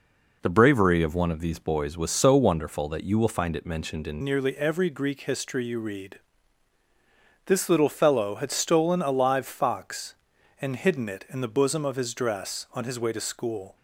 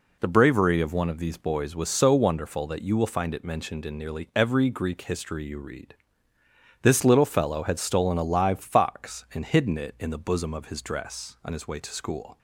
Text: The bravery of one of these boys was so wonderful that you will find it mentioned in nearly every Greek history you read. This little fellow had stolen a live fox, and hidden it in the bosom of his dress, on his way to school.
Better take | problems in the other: second | changes voice at "nearly"; from 4.2 s on; 9.5 s long

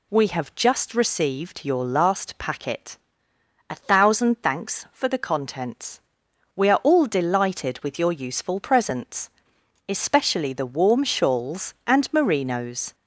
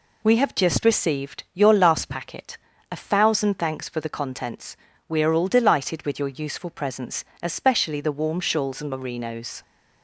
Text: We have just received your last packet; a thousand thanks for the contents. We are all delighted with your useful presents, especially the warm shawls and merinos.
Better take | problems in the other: second | gets louder; slight; throughout; 2 dB

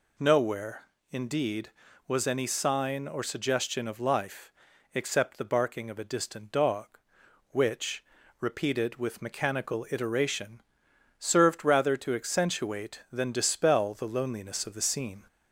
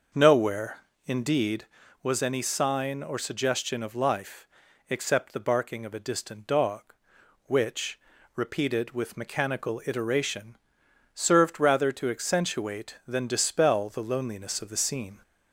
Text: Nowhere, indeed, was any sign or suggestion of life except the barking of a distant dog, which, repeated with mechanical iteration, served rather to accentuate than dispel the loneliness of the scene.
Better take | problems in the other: first | starts louder than the rest; noticeable; until 1.6 s; 6 dB // pauses between "life" and "except"; at 4.4 s; 0.42 s long; also in the first

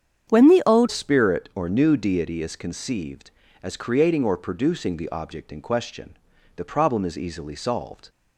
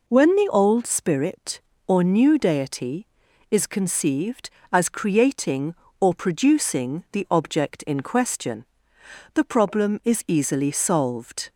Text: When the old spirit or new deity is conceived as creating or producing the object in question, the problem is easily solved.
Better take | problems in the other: second | starts louder than the rest; strong; until 1.3 s; 8.5 dB // changes voice at "spirit"; from 0.8 s on; 7.2 s long

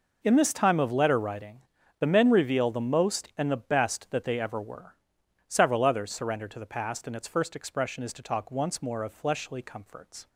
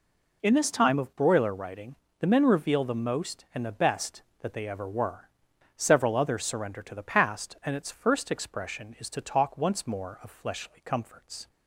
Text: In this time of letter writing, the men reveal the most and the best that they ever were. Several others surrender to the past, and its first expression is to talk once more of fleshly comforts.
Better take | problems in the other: first | says "broiler" for "letter"; at 1.1 s

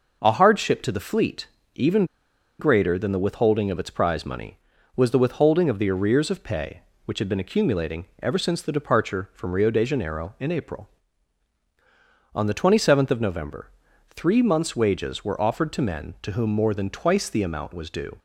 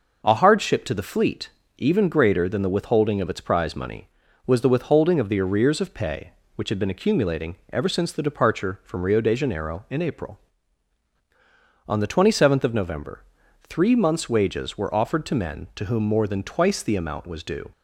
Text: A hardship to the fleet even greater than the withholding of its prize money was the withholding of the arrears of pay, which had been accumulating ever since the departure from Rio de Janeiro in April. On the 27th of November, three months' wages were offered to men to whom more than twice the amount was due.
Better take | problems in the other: second | pauses between "fleet" and "even"; slight; at 1.4 s; 0.30 s long; slight in the second // pauses between "even" and "greater"; noticeable; at 2.0 s; 0.54 s long // pauses between "accumulating" and "ever"; slight; at 8.0 s; 0.18 s long; slight in the second

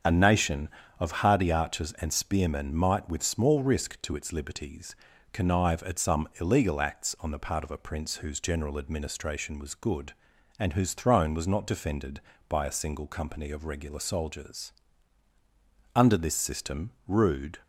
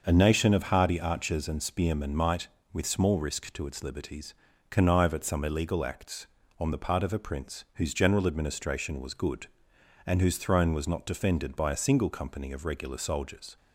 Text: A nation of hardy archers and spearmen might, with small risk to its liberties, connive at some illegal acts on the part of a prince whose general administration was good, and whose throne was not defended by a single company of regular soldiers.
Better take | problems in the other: second | starts louder than the rest; strong; until 1.3 s; 7.5 dB; also in the second // goes on to say "Under this system rude"; from 15.9 s on; 1.6 s long

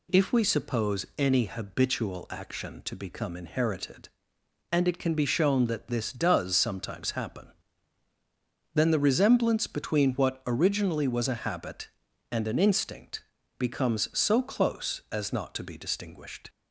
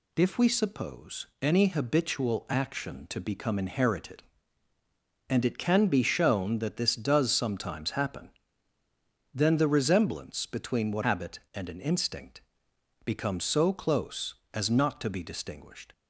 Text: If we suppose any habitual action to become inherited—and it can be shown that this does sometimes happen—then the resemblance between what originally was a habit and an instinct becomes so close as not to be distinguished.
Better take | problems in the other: first | pauses between "suppose" and "any"; slight; at 1.2 s; 0.16 s long // skips "originally was a"; at 11.0 s // pauses between "instinct" and "becomes"; noticeable; at 12.3 s; 0.64 s long; also in the first

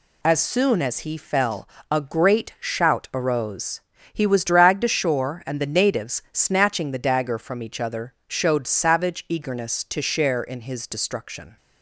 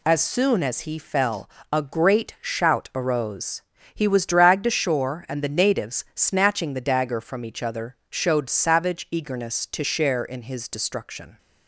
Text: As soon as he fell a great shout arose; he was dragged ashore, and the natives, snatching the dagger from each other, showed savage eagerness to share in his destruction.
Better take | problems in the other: neither | pauses between "fell" and "a"; slight; the same in both

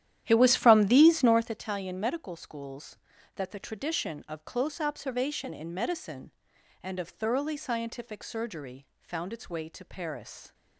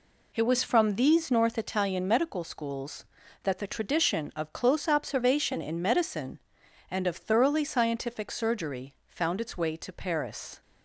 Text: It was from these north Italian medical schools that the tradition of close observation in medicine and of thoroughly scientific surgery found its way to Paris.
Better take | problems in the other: second | starts louder than the rest; strong; until 1.6 s; 11.5 dB

